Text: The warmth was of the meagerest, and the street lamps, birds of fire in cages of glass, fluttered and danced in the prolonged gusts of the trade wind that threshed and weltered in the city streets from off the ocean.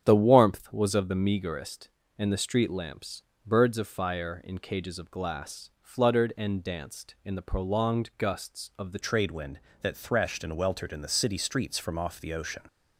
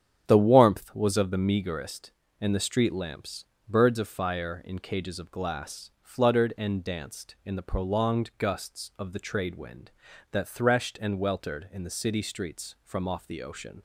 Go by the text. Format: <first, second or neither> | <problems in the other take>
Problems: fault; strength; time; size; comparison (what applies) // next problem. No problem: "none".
second | starts louder than the rest; strong; until 1.1 s; 9.5 dB; strong in the second // changes voice at "trade"; from 9.0 s on; 3.6 s long